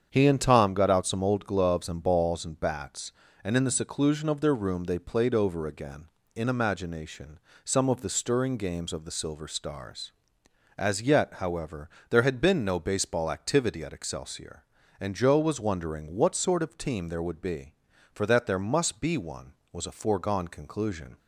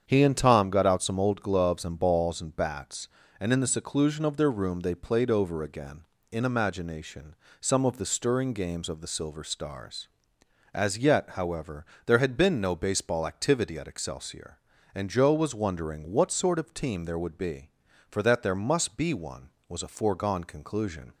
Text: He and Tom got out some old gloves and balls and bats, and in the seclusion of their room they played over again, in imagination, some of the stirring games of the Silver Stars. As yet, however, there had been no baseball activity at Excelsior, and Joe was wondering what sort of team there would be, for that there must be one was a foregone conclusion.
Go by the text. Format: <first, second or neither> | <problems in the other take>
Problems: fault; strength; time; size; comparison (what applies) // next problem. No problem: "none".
neither | starts louder than the rest; strong; the same in both